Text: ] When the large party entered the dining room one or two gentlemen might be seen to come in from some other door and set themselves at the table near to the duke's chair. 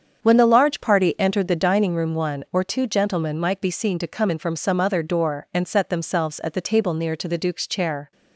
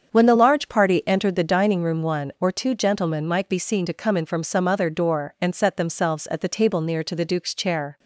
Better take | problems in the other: neither | starts louder than the rest; strong; the same in both

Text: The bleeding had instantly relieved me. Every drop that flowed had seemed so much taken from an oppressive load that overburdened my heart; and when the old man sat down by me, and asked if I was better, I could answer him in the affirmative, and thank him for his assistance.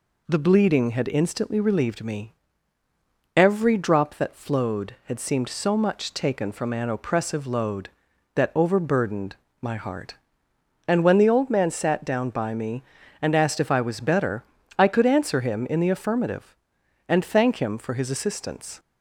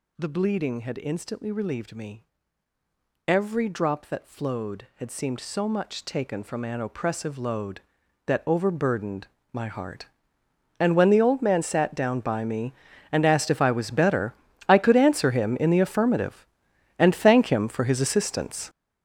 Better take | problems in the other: first | gets louder; strong; throughout; 11 dB // pauses between "overburdened" and "my"; slight; at 9.2 s; 0.24 s long; slight in the first

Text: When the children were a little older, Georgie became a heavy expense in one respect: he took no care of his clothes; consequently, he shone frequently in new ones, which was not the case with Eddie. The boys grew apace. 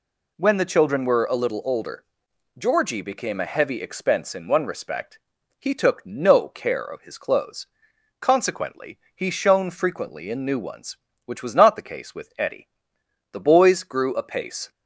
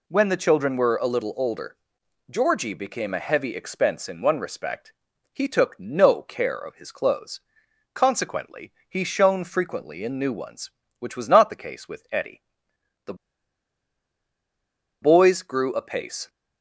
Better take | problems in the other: first | pauses between "The" and "boys"; strong; at 13.1 s; 1.8 s long

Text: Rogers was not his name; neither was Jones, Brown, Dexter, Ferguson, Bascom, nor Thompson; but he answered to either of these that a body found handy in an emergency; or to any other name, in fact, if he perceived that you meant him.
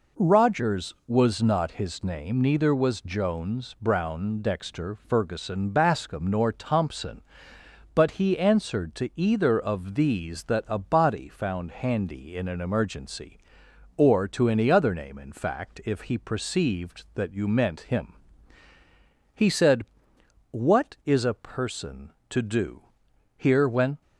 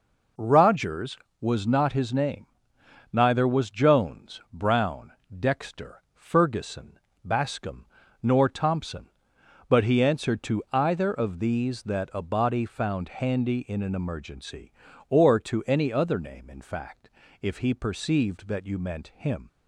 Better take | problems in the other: second | goes on to say "He said What is a person to do here when"; strong; from 19.3 s on; 4.6 s long

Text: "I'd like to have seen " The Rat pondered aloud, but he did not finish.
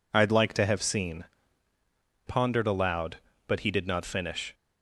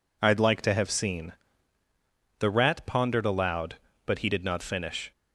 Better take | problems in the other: second | skips "The Rat"; at 2.2 s

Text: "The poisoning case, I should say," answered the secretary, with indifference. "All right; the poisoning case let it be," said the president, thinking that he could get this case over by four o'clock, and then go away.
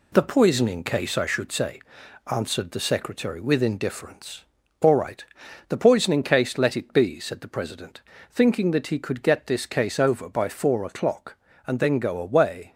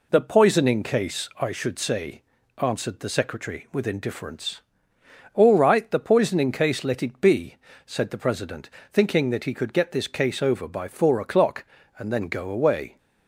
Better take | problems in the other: second | gets quieter; noticeable; throughout; 4.5 dB

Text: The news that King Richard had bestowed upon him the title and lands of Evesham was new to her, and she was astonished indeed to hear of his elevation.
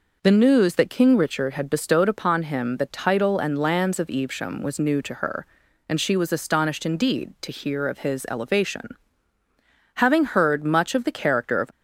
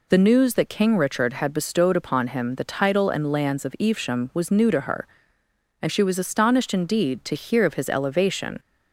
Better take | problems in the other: second | goes on to say "Having heard much of the character of"; strong; from 9.9 s on; 1.7 s long

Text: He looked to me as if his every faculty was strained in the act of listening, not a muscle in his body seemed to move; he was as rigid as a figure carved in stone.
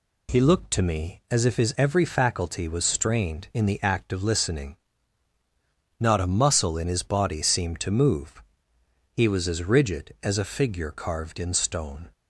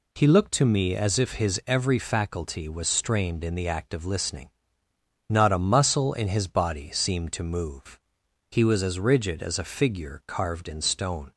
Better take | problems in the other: neither | none

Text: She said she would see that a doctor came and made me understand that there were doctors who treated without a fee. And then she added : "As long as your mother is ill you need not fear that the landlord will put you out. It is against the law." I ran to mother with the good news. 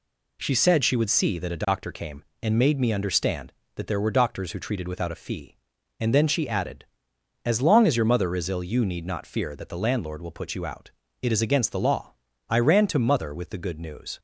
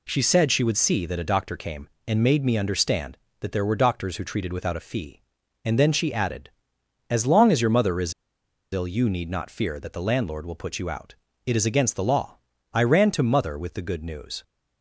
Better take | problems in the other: first | pauses between "is" and "ill"; noticeable; at 8.1 s; 0.59 s long

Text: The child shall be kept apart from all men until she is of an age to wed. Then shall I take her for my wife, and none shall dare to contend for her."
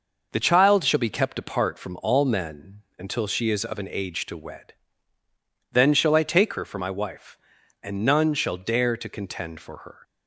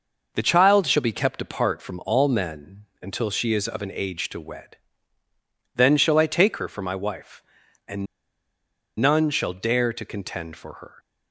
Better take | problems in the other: first | pauses between "men" and "until"; slight; at 2.8 s; 0.18 s long; slight in the first // pauses between "and" and "none"; noticeable; at 8.0 s; 0.94 s long

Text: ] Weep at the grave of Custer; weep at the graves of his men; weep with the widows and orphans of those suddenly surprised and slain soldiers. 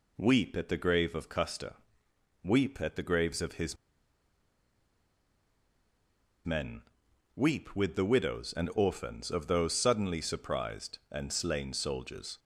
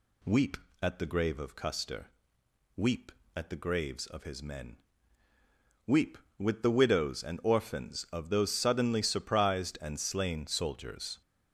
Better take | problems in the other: second | pauses between "his" and "men"; strong; at 3.7 s; 2.7 s long

